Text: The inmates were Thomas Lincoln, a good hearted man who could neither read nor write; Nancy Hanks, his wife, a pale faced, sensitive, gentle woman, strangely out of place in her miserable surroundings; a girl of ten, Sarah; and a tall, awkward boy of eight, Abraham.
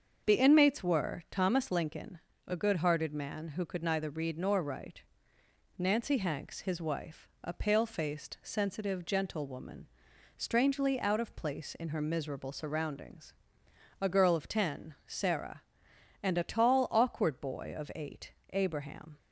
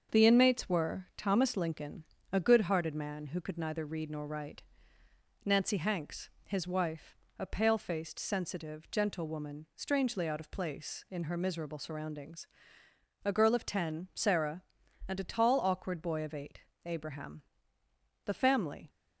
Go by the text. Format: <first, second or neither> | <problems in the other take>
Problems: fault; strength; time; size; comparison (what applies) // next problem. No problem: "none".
first | starts louder than the rest; until 1.2 s; 7 dB; also in the first // goes on to say "The family"; noticeable; from 18.2 s on; 0.64 s long